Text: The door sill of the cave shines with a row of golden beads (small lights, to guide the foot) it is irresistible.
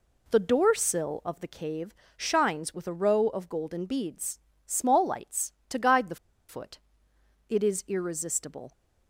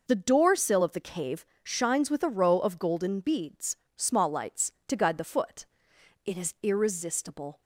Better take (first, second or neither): second